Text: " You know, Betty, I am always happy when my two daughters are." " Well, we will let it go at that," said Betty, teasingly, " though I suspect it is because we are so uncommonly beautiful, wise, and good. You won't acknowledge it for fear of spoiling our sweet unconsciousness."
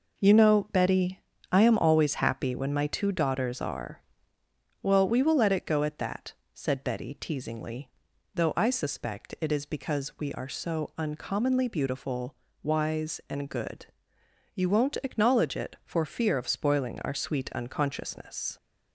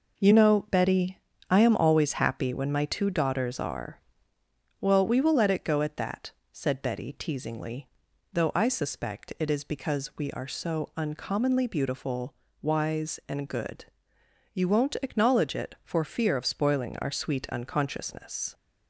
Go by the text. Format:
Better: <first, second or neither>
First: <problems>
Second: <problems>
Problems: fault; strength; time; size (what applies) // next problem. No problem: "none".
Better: neither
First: none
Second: none